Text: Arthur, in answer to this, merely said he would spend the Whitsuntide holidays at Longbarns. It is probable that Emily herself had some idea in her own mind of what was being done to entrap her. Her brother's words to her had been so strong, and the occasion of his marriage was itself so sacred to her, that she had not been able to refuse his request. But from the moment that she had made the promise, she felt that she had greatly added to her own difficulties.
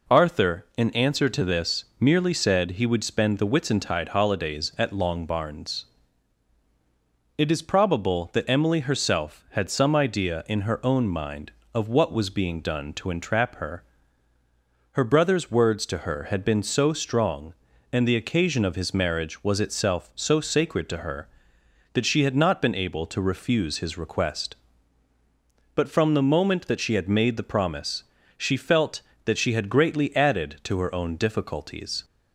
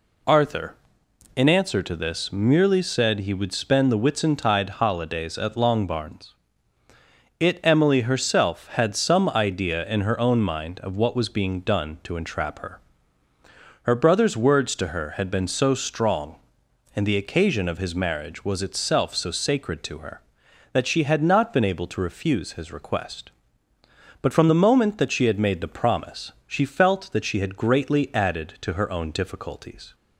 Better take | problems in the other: first | skips "is probable that"; at 7.6 s

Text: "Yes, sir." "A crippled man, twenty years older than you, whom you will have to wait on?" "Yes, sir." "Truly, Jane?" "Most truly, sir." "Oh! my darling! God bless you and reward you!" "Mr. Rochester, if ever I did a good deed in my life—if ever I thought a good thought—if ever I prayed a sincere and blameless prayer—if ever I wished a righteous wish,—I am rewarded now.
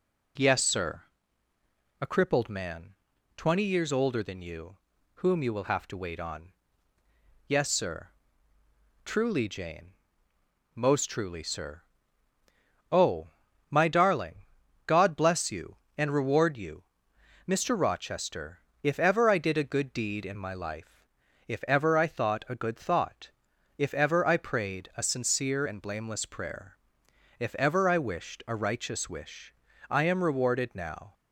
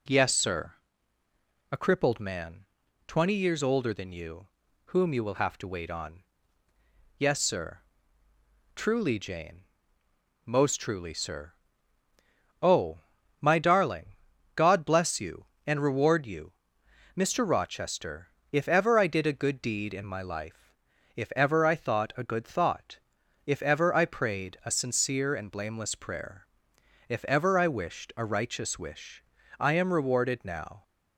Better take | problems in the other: neither | none

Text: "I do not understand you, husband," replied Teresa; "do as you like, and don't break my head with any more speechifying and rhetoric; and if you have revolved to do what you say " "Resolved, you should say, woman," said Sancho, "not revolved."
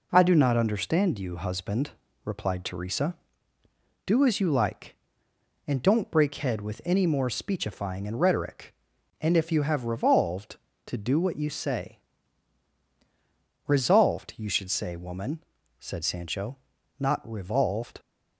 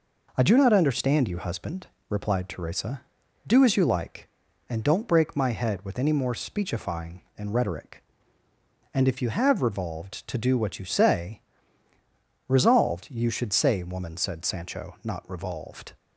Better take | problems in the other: second | skips "my"; at 6.3 s

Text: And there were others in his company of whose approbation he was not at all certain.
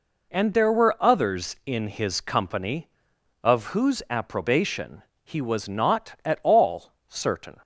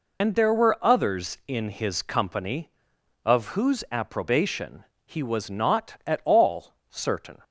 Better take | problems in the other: first | loses the start of "And"; at 0.2 s; 80 ms // pauses between "approbation" and "he"; slight; at 4.8 s; 0.20 s long; slight in the first // pauses between "all" and "certain"; slight; at 6.7 s; 0.16 s long; slight in the first

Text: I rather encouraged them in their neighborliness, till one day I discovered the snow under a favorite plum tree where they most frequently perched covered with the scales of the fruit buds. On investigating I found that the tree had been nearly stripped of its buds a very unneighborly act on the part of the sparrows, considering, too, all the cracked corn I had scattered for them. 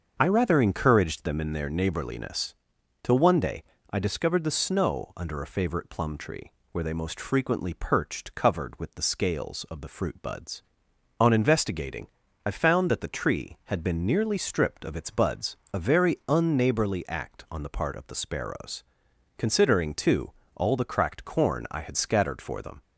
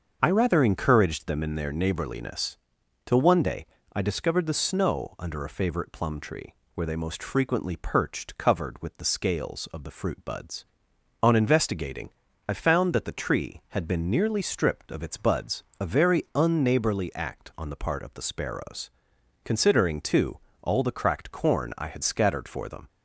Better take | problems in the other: neither | starts louder than the rest; the same in both // pauses between "day" and "I"; slight; the same in both // pauses between "tree" and "where"; slight; the same in both // pauses between "investigating" and "I"; slight; the same in both // pauses between "buds" and "a"; slight; the same in both

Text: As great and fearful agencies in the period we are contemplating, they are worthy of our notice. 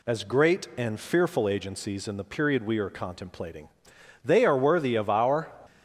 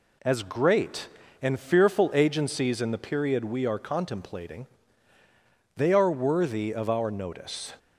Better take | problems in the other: second | stops before "notice"; at 5.6 s

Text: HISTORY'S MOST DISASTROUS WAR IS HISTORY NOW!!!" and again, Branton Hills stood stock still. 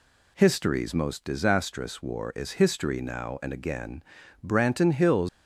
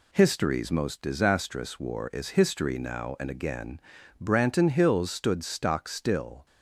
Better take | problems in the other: second | stops before "stood stock still"; at 5.2 s

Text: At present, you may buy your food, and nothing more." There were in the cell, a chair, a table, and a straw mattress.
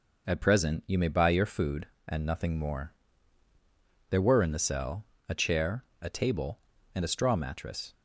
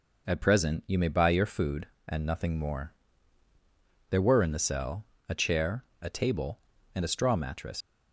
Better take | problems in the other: first | leaves "mattress" unfinished; at 7.8 s; 135 ms

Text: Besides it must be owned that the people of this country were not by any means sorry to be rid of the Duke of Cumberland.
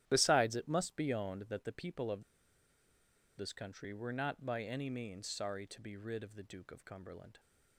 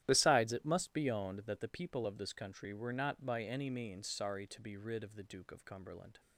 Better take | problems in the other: second | starts louder than the rest; strong; until 1.0 s; 12.5 dB; strong in the second // pauses between "of" and "this"; at 2.2 s; 1.1 s long

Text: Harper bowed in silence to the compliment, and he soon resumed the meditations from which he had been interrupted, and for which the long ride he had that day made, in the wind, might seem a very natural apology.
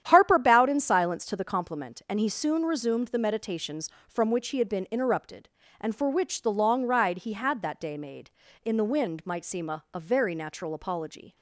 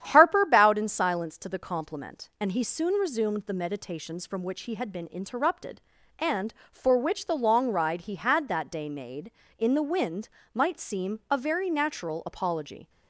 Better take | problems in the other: second | starts louder than the rest; strong; until 1.0 s; 10 dB; strong in the second // says "a" twice; at 9.9 s

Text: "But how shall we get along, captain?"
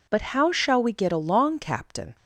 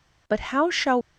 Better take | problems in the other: first | stops before "we get along captain"; at 1.0 s

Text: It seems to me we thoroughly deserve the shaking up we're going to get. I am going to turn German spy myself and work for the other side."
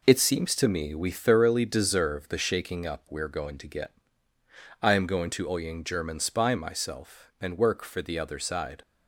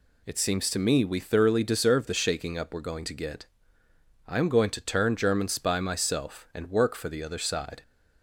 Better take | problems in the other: second | says "oying" for "turn"; at 5.4 s

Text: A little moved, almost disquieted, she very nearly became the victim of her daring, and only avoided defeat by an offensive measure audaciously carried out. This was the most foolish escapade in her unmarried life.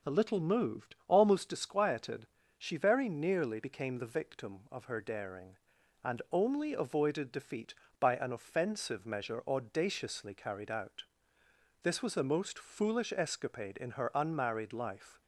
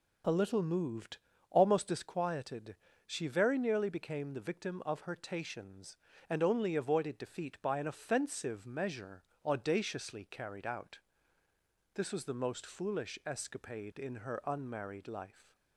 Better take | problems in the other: first | says "tations" for "daring"; at 5.1 s // pauses between "measure" and "audaciously"; slight; at 9.2 s; 0.24 s long

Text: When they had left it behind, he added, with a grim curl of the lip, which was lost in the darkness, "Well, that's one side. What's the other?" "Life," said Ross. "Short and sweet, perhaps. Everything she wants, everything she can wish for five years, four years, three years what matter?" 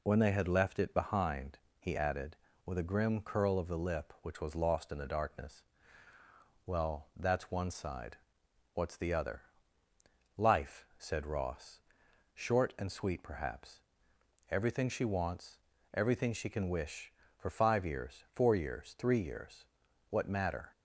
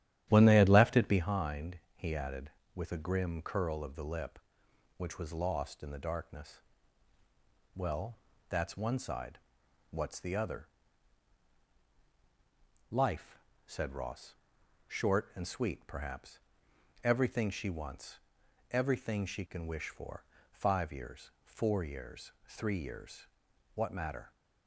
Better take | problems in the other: first | starts louder than the rest; strong; until 1.4 s; 11.5 dB // pauses between "for" and "five"; slight; at 20.2 s; 0.30 s long // pauses between "years" and "what"; noticeable; at 23.2 s; 0.48 s long; noticeable in the first

